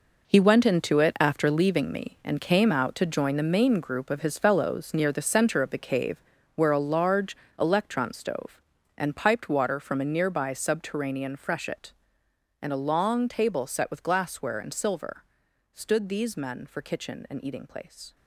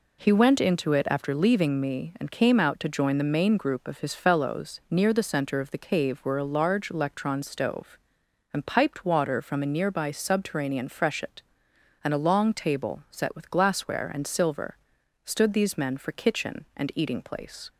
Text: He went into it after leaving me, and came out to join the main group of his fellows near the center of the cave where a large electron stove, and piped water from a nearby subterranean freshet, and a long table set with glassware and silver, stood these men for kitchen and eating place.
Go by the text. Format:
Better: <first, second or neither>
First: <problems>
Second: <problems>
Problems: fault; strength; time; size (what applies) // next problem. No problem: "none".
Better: second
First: gets quieter; strong; throughout; 11.5 dB // pauses between "cave" and "where"; slight; at 6.2 s; 0.34 s long // pauses between "large" and "electron"; slight; at 7.3 s; 0.24 s long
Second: none